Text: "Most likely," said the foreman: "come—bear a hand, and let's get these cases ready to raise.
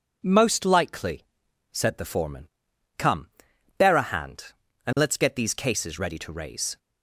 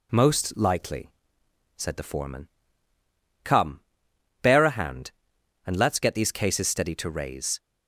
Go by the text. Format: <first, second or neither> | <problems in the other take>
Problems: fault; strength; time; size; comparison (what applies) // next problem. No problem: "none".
first | says "steady" for "ready"; at 6.6 s